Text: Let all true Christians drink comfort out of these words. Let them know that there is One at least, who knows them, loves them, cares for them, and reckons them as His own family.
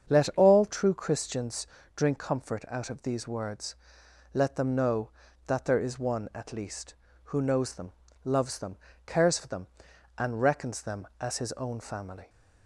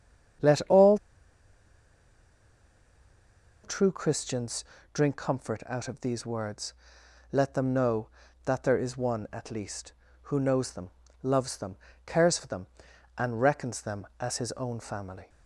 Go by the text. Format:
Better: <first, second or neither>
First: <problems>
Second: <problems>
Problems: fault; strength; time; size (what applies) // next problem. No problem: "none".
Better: first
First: starts louder than the rest; strong; until 1.1 s; 7.5 dB // pauses between "Christians" and "drink"; slight; at 1.6 s; 0.30 s long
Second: starts louder than the rest; strong; until 4.1 s; 7.5 dB // pauses between "all" and "true"; strong; at 0.9 s; 2.6 s long // pauses between "Christians" and "drink"; slight; at 4.6 s; 0.30 s long